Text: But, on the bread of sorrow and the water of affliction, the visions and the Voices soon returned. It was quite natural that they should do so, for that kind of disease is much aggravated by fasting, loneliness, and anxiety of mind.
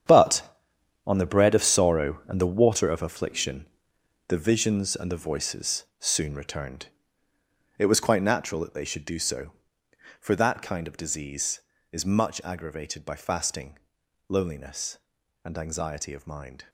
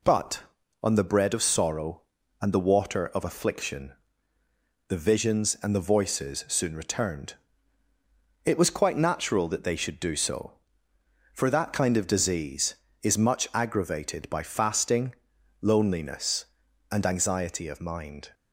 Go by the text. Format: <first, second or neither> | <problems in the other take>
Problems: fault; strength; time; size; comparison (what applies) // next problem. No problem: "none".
second | gets quieter; strong; throughout; 13 dB // pauses between "Voices" and "soon"; slight; at 5.8 s; 0.16 s long